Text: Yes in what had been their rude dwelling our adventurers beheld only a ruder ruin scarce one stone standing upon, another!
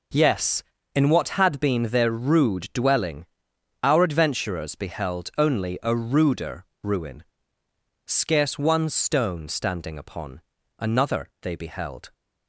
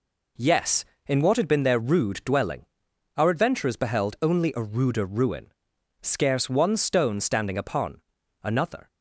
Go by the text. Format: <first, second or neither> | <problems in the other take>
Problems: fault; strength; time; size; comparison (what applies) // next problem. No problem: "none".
second | pauses between "dwelling" and "our"; noticeable; at 3.2 s; 0.58 s long; noticeable in the second // pauses between "ruder" and "ruin"; slight; at 6.6 s; 0.20 s long // pauses between "ruin" and "scarce"; noticeable; at 7.2 s; 0.82 s long; noticeable in the second // goes on to say "They beheld"; noticeable; from 11.4 s on; 0.72 s long